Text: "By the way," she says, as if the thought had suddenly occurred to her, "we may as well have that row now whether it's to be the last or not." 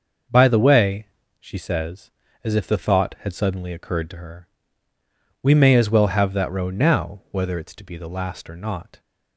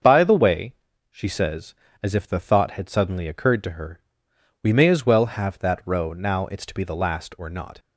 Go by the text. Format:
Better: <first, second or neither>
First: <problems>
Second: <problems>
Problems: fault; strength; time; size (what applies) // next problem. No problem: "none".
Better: first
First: starts louder than the rest; noticeable; until 1.6 s; 6 dB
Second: starts louder than the rest; until 1.3 s; 6.5 dB // skips "whether"; at 6.4 s